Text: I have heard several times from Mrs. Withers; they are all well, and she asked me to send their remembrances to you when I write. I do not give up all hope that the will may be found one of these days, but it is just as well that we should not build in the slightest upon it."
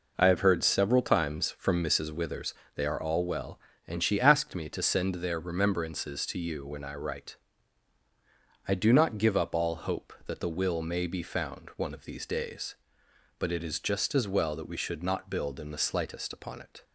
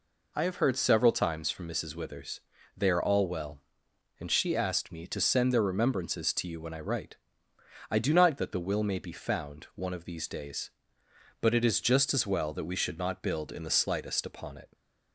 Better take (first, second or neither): first